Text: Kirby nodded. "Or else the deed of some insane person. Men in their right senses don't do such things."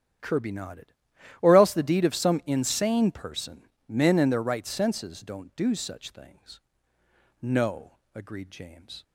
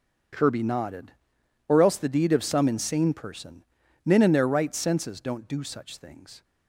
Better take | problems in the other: second | starts louder than the rest; strong; until 1.7 s; 9.5 dB; also in the second // goes on to say "No agreed James"; from 7.3 s on; 1.6 s long

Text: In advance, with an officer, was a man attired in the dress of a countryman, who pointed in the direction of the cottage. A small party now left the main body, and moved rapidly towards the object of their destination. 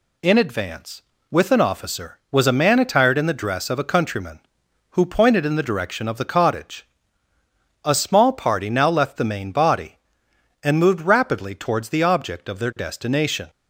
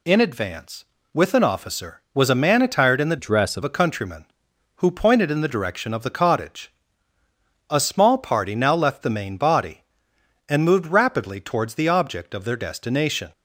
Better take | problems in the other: first | changes voice from "dress" to "of"; from 3.1 to 3.6 s; 0.5 s long

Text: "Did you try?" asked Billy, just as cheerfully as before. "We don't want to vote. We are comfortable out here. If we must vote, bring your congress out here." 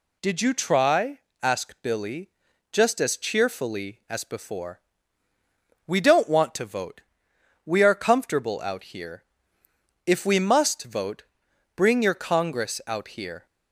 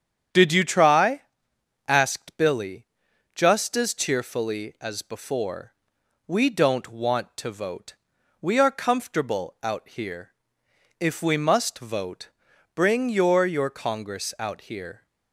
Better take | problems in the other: first | starts louder than the rest; strong; until 1.9 s; 8.5 dB // says "your" twice; at 13.4 s

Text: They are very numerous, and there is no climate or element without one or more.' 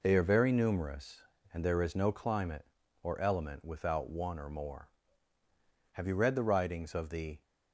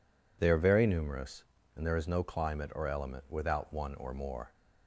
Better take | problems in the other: second | goes on to say "Have you read the writings of the"; from 5.9 s on; 1.5 s long

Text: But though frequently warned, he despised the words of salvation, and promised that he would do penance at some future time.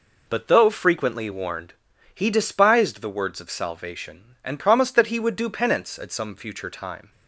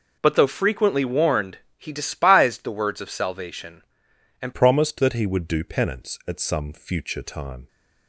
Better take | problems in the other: first | changes voice at "promised"; from 4.5 s on; 3.1 s long

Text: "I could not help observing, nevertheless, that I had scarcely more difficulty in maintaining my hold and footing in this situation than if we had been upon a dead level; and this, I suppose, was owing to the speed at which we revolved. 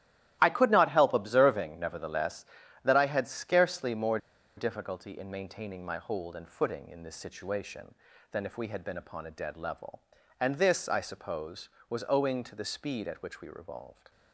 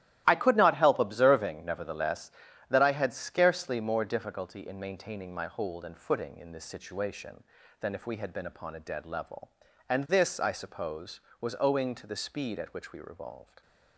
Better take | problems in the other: second | starts louder than the rest; strong; until 1.4 s; 14 dB; strong in the second // pauses between "more" and "difficulty"; at 4.1 s; 0.39 s long

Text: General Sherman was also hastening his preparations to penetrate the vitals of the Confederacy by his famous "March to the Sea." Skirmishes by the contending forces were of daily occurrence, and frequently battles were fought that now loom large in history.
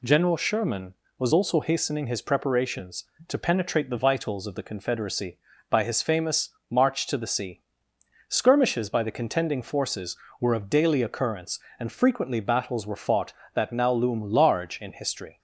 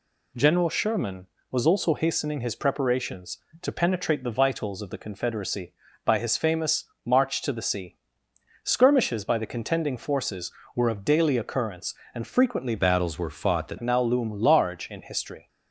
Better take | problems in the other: first | pauses between "famous" and "March"; slight; at 6.8 s; 0.20 s long; slight in the first // changes voice from "battles" to "that"; from 12.7 to 13.7 s; 1.0 s long

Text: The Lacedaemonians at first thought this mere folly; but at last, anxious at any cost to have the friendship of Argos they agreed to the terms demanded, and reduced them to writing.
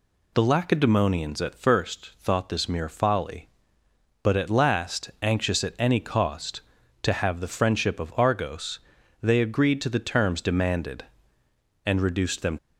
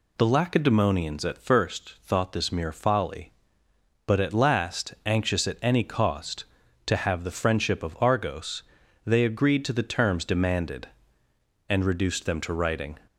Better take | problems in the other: second | pauses between "Argos" and "they"; at 8.7 s; 0.42 s long; also in the second // stops before "to writing"; at 12.5 s

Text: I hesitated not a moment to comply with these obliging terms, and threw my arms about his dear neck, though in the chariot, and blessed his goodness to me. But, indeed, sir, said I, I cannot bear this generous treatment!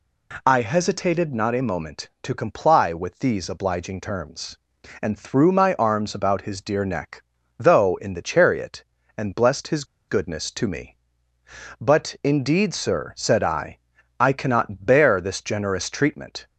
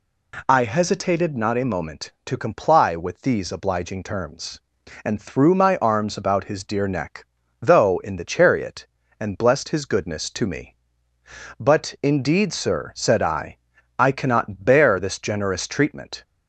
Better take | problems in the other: second | pauses between "his" and "goodness"; slight; at 9.8 s; 0.25 s long

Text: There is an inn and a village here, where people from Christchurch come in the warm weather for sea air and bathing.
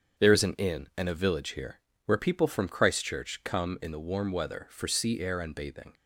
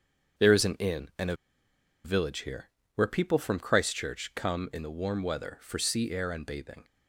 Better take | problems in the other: first | starts louder than the rest; strong; until 2.1 s; 7.5 dB; strong in the first // pauses between "a" and "village"; noticeable; at 1.3 s; 0.68 s long

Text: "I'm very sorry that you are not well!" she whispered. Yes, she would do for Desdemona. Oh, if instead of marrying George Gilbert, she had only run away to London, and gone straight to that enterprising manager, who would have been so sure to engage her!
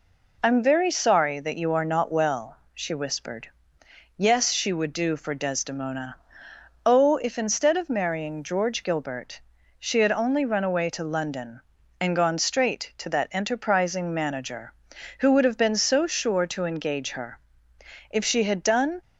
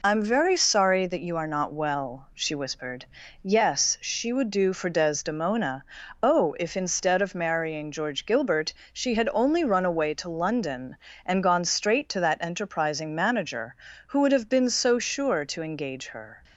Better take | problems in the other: second | goes on to say "If she had done"; noticeable; from 18.1 s on; 0.90 s long

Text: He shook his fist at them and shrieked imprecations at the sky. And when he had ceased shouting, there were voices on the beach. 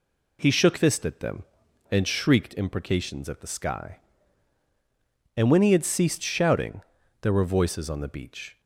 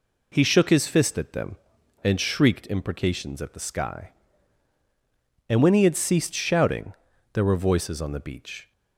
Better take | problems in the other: second | skips "his"; at 0.7 s

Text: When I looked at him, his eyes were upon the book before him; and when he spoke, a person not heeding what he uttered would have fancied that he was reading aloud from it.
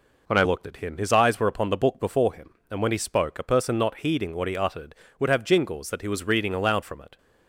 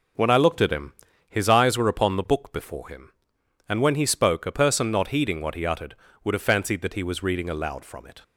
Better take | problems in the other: second | says "jingles" for "fancied"; at 5.4 s

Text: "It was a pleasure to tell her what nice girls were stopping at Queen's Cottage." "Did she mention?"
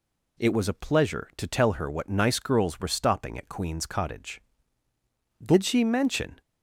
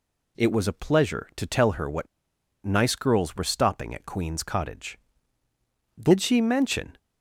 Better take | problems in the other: first | pauses between "what" and "nice"; noticeable; at 2.0 s; 0.58 s long

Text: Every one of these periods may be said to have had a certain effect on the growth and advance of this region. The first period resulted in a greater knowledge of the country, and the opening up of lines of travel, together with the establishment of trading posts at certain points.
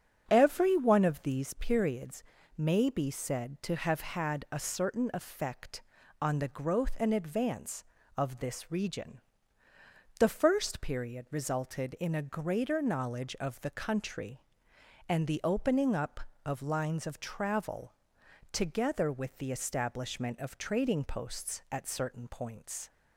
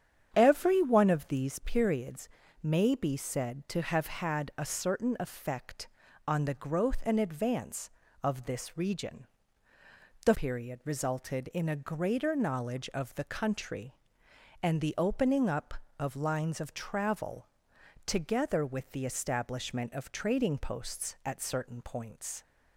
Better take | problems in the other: first | starts louder than the rest; strong; until 1.3 s; 8.5 dB; strong in the first // pauses between "periods" and "may"; slight; at 2.2 s; 0.34 s long; slight in the first // skips "first"; at 10.3 s

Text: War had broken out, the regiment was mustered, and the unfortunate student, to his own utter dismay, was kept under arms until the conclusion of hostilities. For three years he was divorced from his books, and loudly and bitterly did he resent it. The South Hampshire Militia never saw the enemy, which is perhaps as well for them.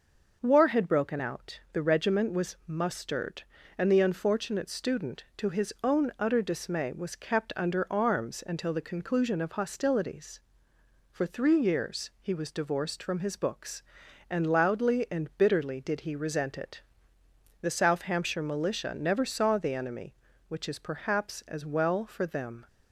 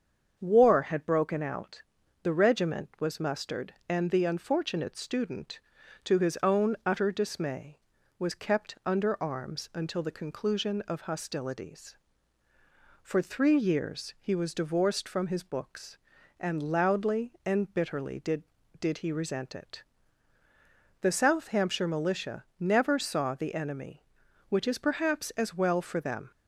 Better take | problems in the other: first | starts louder than the rest; strong; until 1.4 s; 7 dB // says "did" twice; at 18.7 s

